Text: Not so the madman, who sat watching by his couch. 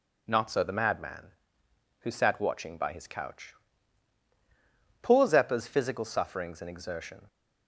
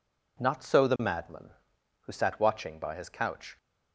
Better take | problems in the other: second | goes on to say "Poor Zeppa's physical sufferings and exertion"; strong; from 5.0 s on; 2.2 s long

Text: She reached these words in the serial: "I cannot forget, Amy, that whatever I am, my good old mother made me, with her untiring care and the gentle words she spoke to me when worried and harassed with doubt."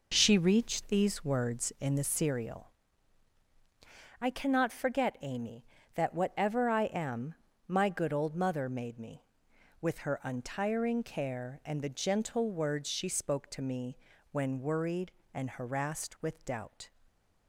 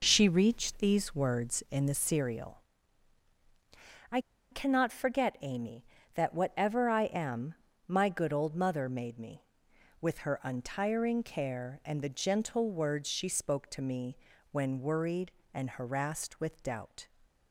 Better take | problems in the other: first | pauses between "I" and "cannot"; slight; at 4.1 s; 0.32 s long // pauses between "me" and "when"; slight; at 14.1 s; 0.36 s long; slight in the first

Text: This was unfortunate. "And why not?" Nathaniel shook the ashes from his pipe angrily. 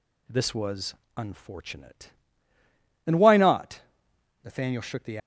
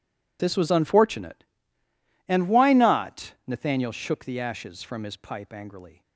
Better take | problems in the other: second | pauses between "was" and "unfortunate"; slight; at 0.9 s; 0.24 s long // stops before "ashes from his pipe angrily"; at 5.1 s

